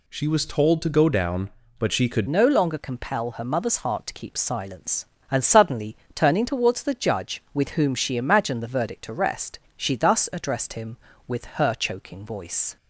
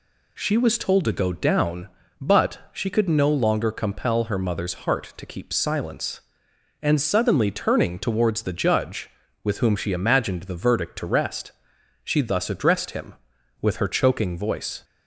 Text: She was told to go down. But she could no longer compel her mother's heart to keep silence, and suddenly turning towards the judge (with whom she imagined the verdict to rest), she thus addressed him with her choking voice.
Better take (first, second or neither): second